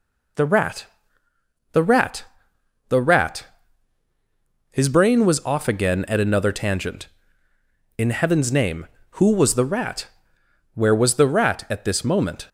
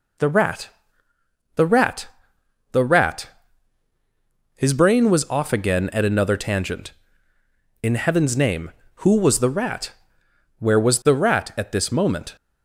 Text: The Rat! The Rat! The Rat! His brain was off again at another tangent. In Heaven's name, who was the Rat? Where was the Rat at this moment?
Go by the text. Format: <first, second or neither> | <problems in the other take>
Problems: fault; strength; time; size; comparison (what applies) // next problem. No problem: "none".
neither | none